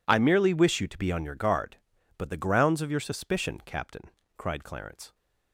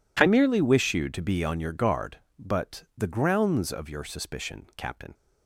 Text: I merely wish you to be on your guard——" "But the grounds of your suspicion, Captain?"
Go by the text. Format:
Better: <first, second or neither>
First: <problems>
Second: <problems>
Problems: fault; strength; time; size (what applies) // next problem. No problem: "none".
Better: second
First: goes on to say "cried Clarence"; noticeable; from 4.3 s on; 0.78 s long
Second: none